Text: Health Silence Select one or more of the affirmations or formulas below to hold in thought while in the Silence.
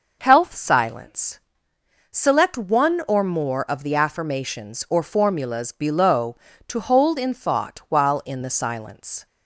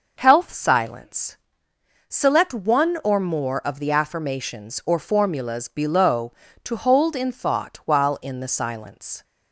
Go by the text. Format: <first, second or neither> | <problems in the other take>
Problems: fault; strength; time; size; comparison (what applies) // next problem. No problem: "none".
neither | pauses between "Silence" and "Select"; noticeable; the same in both